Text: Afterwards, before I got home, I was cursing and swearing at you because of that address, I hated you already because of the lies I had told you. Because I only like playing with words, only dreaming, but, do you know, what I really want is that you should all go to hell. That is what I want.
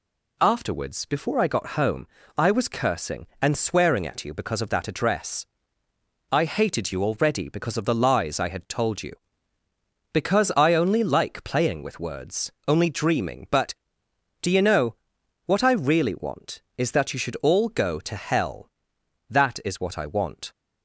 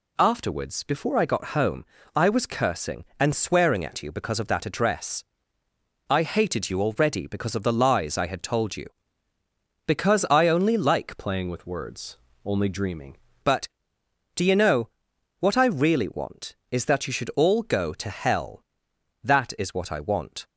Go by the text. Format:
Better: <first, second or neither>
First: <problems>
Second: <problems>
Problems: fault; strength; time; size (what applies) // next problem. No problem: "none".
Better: first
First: none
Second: changes voice from "playing" to "dreaming"; from 11.1 to 13.1 s; 2.0 s long